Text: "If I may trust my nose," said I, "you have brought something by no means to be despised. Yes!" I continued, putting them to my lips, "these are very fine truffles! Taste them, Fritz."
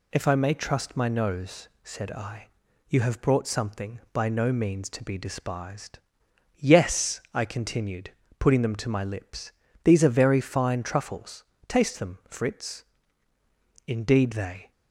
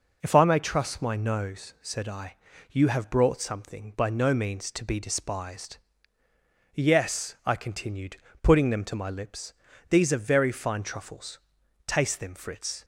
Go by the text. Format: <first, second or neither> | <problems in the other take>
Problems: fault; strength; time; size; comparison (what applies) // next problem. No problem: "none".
second | goes on to say "Indeed they"; noticeable; from 13.8 s on; 0.84 s long